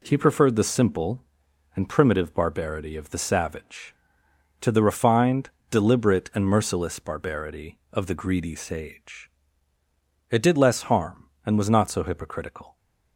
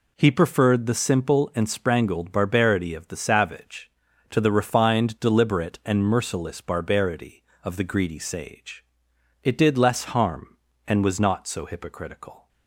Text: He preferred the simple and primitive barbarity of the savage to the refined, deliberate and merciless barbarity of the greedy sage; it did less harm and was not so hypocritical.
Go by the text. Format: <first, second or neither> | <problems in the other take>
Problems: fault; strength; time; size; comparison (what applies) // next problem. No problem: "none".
first | says "sprangled" for "primitive"; at 1.6 s